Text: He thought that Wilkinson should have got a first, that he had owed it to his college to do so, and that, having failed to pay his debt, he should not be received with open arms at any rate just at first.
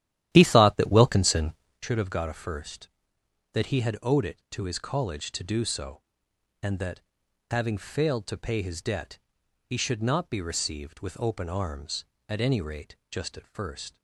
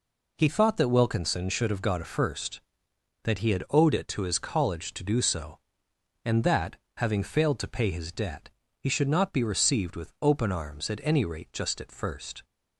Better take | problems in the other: second | starts louder than the rest; strong; until 1.9 s; 12 dB // pauses between "rate" and "just"; slight; at 12.9 s; 0.16 s long

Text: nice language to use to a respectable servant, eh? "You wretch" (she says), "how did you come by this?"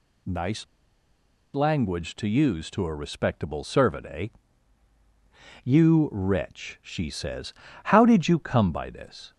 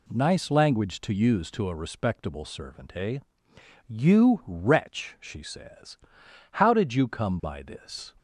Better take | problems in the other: second | pauses between "nice" and "language"; noticeable; at 0.6 s; 0.90 s long

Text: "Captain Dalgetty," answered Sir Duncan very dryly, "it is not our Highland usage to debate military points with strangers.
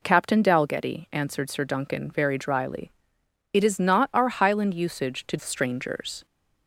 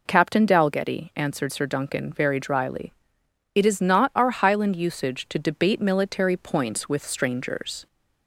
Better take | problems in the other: second | skips "debate military points with"; at 5.3 s

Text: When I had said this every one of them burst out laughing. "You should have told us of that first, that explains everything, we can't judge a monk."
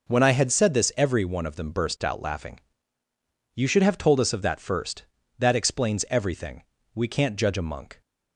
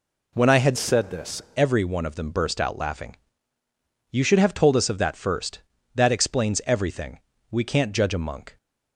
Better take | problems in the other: first | changes voice from "said" to "this"; from 0.7 to 1.4 s; 0.7 s long

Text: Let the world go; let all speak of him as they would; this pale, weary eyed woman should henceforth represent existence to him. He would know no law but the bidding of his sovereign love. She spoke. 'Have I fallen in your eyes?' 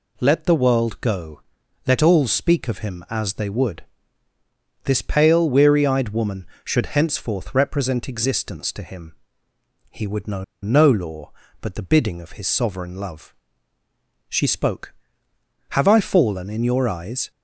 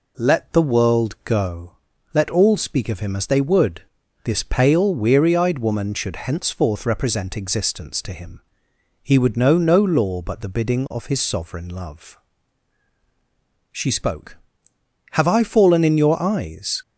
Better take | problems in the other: second | pauses between "know" and "no"; slight; at 10.4 s; 0.20 s long

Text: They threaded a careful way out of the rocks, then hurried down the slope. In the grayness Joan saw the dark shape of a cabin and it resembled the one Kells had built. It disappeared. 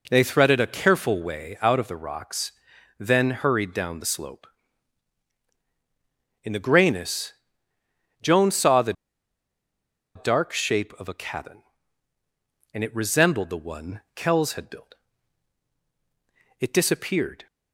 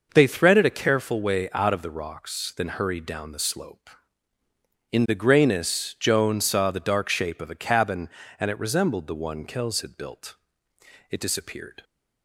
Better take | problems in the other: second | pauses between "grayness" and "Joan"; noticeable; at 7.3 s; 0.90 s long // pauses between "the" and "dark"; at 8.9 s; 1.2 s long

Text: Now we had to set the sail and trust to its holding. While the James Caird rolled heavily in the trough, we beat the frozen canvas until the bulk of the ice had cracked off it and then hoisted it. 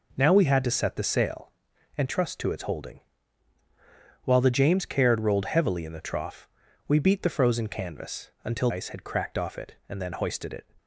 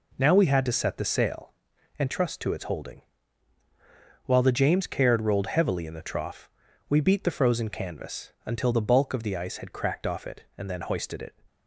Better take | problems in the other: second | skips "the bulk of the"; at 8.7 s

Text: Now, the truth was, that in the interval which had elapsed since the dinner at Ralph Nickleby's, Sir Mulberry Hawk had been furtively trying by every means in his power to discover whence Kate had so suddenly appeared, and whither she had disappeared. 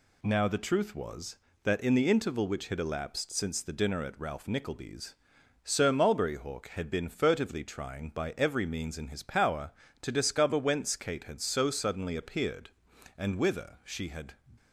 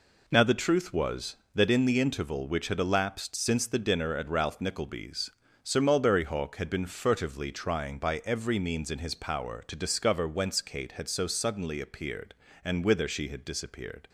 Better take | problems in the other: second | stops before "disappeared"; at 14.5 s

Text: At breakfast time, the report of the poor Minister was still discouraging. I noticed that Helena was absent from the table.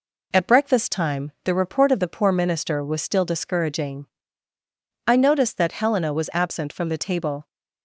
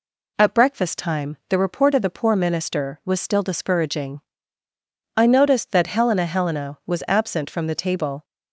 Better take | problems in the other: first | says "Helena" twice; at 6.2 s

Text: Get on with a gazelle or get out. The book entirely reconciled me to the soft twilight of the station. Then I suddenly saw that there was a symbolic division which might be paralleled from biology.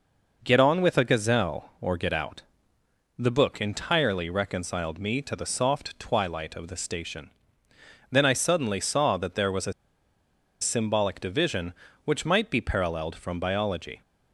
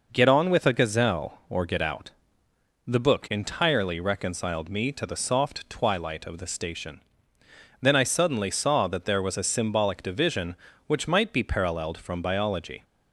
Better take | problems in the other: second | pauses between "a" and "symbolic"; noticeable; at 9.7 s; 0.88 s long

